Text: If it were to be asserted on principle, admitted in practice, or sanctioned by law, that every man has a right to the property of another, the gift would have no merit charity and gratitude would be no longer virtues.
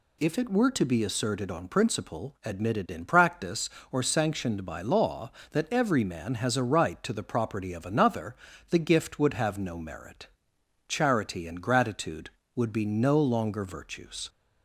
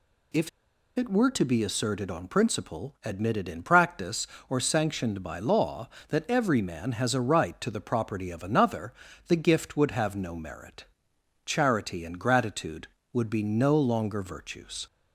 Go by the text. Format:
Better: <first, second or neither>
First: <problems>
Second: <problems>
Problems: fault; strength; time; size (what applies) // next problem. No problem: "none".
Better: first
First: pauses between "merit" and "charity"; noticeable; at 10.2 s; 0.60 s long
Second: pauses between "If" and "it"; noticeable; at 0.4 s; 0.47 s long // pauses between "merit" and "charity"; noticeable; at 10.8 s; 0.60 s long